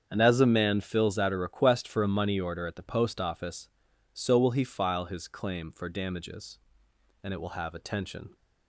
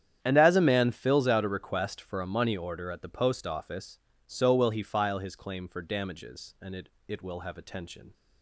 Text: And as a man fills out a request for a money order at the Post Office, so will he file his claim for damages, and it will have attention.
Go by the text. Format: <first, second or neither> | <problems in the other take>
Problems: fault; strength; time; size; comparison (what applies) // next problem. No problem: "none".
first | starts louder than the rest; strong; until 1.2 s; 9.5 dB; strong in the first // says "it" twice; at 7.0 s